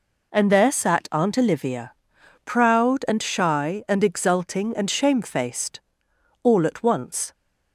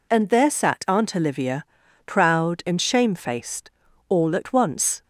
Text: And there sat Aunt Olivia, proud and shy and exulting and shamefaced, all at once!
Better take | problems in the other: first | skips "and shy and exulting"; at 2.6 s

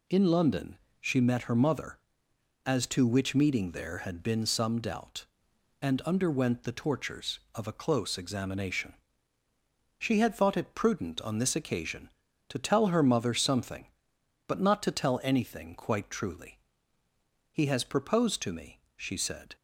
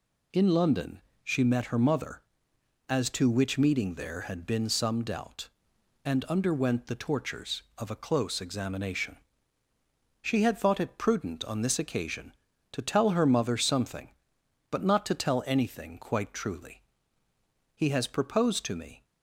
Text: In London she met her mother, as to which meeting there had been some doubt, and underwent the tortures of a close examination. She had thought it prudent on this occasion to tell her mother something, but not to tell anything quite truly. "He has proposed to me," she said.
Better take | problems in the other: first | pauses between "London" and "she"; slight; at 1.0 s; 0.22 s long; slight in the first // stops before "she said"; at 19.0 s

